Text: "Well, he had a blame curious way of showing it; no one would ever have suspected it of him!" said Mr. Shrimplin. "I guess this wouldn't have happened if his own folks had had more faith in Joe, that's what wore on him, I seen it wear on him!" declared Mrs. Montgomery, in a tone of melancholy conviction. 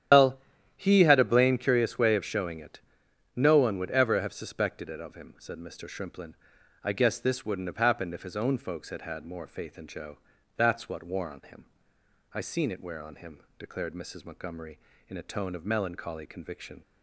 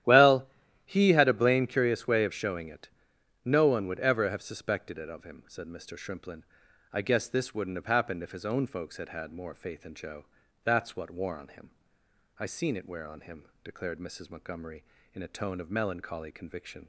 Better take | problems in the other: second | loses the start of "Well"; at 0.1 s; 145 ms // starts louder than the rest; strong; until 1.5 s; 10.5 dB; strong in the second

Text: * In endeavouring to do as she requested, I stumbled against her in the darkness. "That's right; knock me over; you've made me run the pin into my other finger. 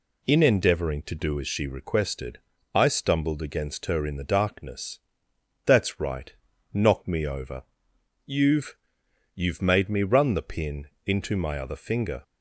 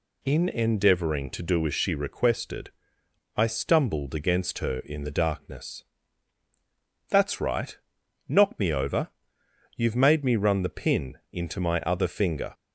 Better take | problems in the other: second | says "you've" twice; at 9.3 s // pauses between "pin" and "into"; slight; at 10.8 s; 0.18 s long

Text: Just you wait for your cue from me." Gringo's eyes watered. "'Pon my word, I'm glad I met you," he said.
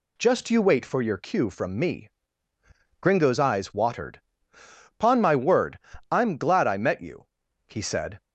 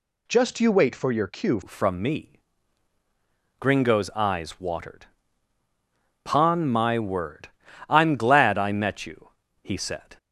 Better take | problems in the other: first | changes voice at "from"; from 1.6 s on; 8.5 s long

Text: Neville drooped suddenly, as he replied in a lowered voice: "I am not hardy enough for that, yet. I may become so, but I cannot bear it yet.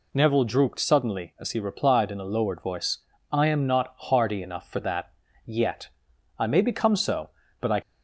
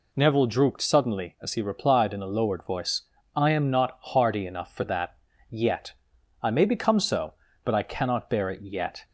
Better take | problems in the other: second | stops before "cannot bear it yet"; at 7.8 s

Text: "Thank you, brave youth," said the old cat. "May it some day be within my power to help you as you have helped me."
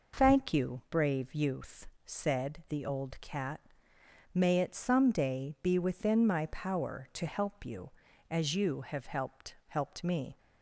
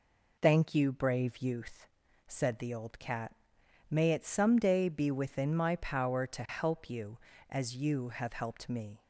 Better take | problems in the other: second | says "helped" twice; at 9.6 s

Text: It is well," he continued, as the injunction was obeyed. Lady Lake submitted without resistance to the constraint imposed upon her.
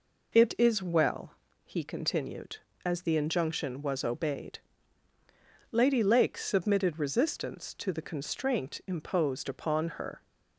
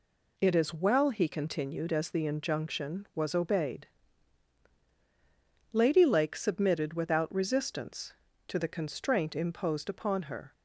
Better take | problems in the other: second | skips "without"; at 6.9 s

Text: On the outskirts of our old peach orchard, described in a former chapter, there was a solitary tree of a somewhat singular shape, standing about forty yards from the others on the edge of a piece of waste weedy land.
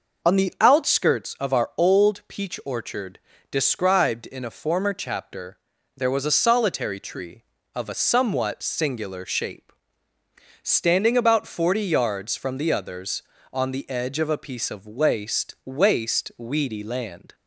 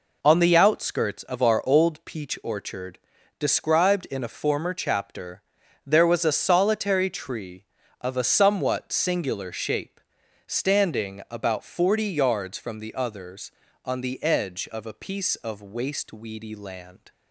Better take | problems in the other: second | says "waste" twice; at 15.6 s

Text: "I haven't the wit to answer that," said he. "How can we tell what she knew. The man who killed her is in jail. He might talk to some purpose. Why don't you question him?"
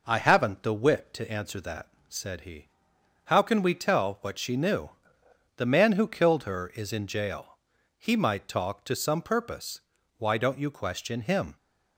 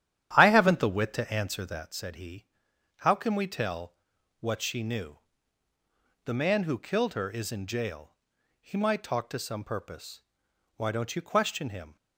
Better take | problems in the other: first | starts louder than the rest; strong; until 2.1 s; 10.5 dB // pauses between "tell" and "what"; at 3.9 s; 0.44 s long

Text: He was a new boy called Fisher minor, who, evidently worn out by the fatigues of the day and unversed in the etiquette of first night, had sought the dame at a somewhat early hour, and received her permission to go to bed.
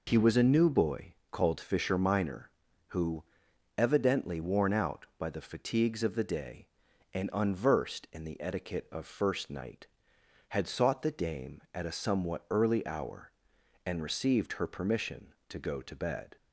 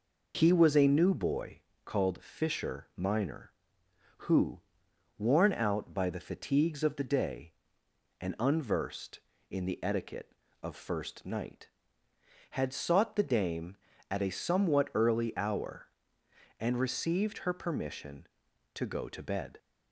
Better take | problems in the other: first | pauses between "boy" and "called"; slight; at 1.5 s; 0.26 s long; slight in the first // skips "evidently"; at 4.8 s

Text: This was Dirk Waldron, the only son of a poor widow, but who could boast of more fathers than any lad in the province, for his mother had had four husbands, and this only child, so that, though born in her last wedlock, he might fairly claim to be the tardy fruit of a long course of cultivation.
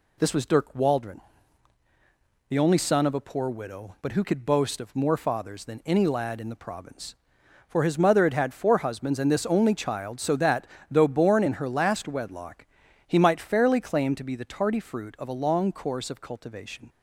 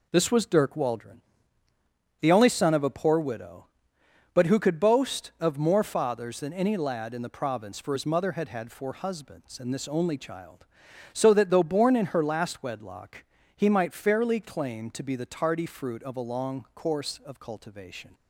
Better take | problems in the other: neither | none

